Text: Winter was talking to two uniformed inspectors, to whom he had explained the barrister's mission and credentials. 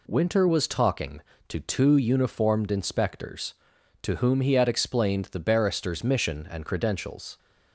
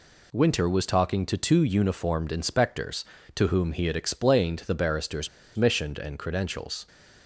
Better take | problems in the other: first | pauses between "barrister's" and "mission"; slight; at 5.2 s; 0.26 s long

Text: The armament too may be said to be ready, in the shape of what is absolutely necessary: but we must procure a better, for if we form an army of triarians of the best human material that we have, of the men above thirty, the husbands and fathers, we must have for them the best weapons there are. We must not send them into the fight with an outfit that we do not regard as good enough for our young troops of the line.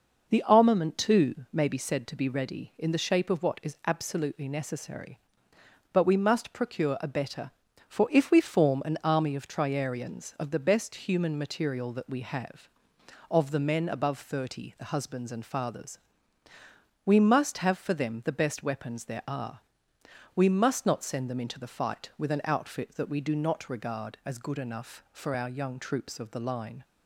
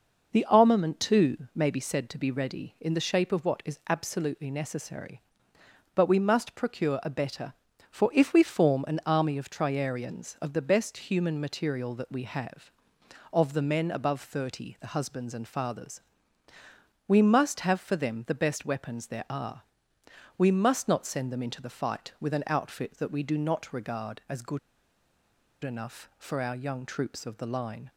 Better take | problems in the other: first | pauses between "good" and "enough"; at 24.5 s; 1.0 s long

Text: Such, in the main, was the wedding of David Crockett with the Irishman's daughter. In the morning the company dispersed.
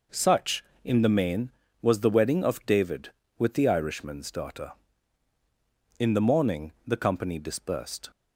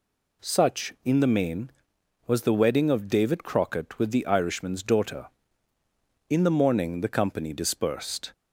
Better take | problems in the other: second | skips "Crockett"; at 3.2 s

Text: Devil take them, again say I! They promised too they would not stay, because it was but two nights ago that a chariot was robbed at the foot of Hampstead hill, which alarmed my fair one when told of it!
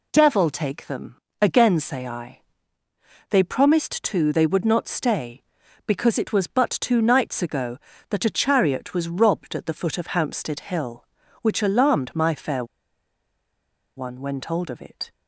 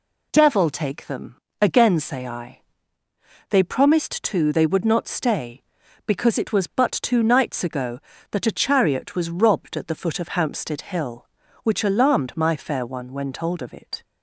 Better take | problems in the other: second | pauses between "fair" and "one"; strong; at 12.6 s; 1.3 s long

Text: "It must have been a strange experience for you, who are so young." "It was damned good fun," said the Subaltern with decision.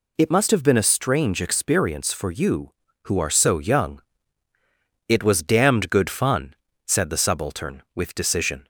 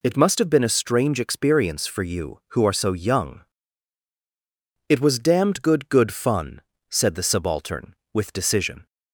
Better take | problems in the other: first | says "good" twice; at 5.8 s

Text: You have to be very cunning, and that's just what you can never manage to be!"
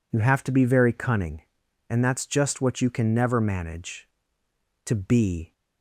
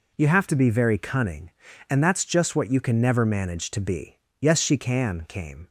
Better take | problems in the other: first | goes on to say "Yes she can came"; from 4.3 s on; 1.3 s long

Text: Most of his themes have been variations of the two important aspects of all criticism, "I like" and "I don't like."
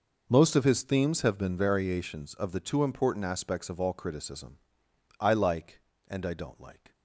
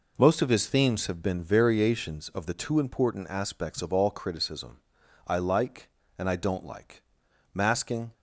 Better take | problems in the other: first | goes on to say "Masking"; from 7.5 s on; 0.60 s long

